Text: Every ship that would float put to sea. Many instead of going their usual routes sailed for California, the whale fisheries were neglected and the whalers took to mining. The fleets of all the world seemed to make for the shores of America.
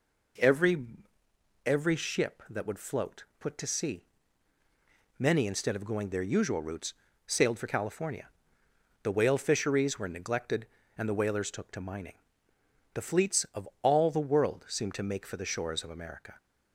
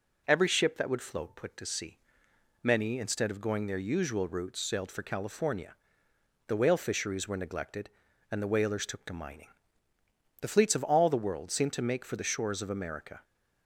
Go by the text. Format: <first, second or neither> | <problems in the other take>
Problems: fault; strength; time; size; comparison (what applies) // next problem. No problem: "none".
second | says "Every" twice; at 1.6 s // pauses between "float" and "put"; slight; at 3.2 s; 0.16 s long // pauses between "routes" and "sailed"; slight; at 6.9 s; 0.34 s long // pauses between "of" and "all"; slight; at 13.6 s; 0.16 s long